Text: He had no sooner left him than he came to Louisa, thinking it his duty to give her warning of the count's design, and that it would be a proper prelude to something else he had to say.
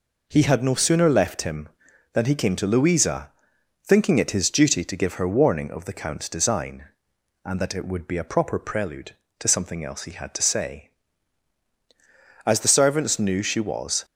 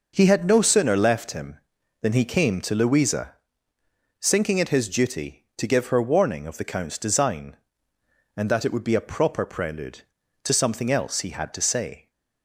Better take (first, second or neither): second